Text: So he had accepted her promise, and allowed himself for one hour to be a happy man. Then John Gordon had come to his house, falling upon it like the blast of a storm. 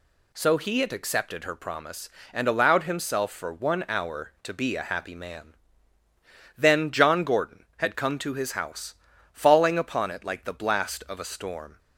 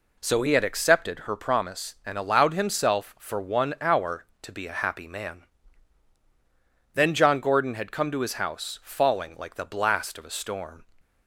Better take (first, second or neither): first